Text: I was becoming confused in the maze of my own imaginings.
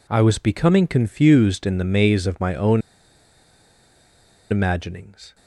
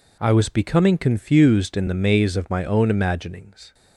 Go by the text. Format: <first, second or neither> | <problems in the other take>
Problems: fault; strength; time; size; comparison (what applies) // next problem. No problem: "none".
second | pauses between "own" and "imaginings"; strong; at 2.8 s; 1.6 s long